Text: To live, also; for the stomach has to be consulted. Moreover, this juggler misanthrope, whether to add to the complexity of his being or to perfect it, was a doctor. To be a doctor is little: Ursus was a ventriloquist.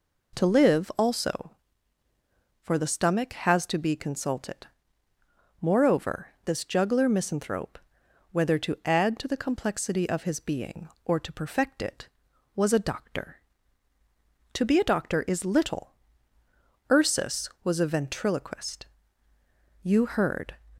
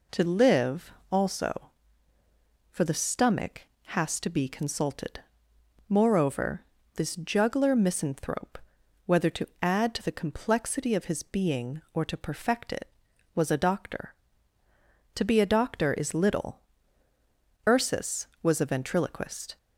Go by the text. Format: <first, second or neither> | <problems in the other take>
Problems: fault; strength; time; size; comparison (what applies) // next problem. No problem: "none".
second | goes on to say "You heard"; noticeable; from 19.8 s on; 0.74 s long